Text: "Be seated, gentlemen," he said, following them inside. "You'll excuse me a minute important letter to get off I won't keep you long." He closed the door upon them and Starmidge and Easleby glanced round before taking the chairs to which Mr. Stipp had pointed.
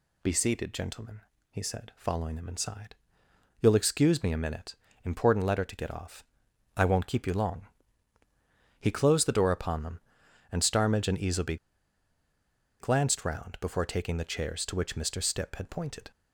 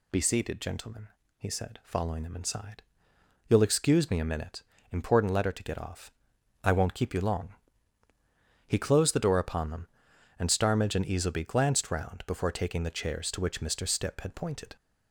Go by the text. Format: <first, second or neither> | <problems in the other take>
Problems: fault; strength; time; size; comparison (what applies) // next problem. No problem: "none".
second | pauses between "minute" and "important"; slight; at 4.7 s; 0.28 s long; slight in the second // pauses between "off" and "I"; noticeable; at 6.2 s; 0.54 s long; noticeable in the second // pauses between "Easleby" and "glanced"; at 11.5 s; 1.2 s long